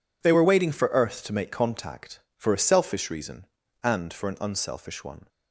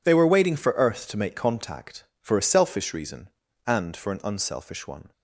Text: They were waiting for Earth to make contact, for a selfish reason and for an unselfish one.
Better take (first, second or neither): neither